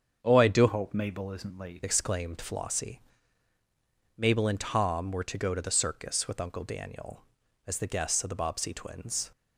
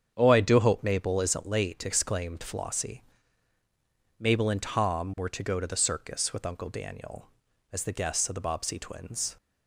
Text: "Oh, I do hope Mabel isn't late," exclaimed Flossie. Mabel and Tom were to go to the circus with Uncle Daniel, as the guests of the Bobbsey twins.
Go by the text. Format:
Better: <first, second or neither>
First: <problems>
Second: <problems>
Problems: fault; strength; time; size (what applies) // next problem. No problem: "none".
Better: second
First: starts louder than the rest; strong; until 1.2 s; 7.5 dB // changes voice from "hope" to "late"; from 0.6 to 1.8 s; 1.2 s long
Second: starts louder than the rest; strong; until 1.1 s; 8 dB